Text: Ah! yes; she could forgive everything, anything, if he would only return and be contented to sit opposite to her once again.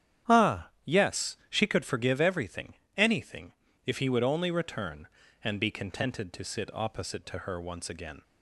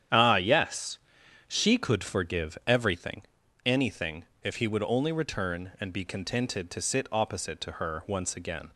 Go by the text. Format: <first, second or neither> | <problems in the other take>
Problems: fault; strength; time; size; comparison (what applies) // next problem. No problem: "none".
neither | starts louder than the rest; strong; the same in both